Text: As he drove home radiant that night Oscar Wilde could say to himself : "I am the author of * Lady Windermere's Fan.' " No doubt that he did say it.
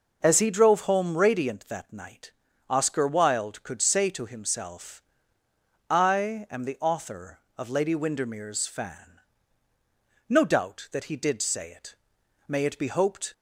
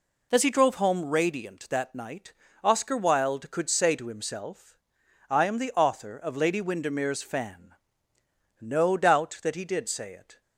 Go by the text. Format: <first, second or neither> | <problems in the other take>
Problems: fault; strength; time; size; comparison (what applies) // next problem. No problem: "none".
second | starts louder than the rest; until 1.2 s; 7 dB // pauses between "night" and "Oscar"; at 2.3 s; 0.38 s long; slight in the second // goes on to say "May it be hoped"; noticeable; from 12.4 s on; 0.86 s long